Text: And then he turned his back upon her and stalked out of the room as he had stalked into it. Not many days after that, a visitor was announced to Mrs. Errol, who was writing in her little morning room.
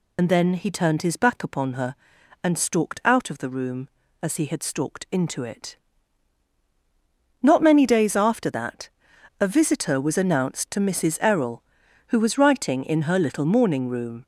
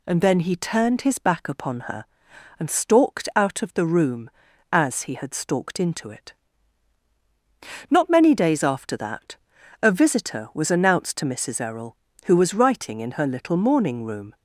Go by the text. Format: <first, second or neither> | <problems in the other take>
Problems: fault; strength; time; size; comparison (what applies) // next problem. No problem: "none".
second | loses the start of "And"; at 0.1 s; 60 ms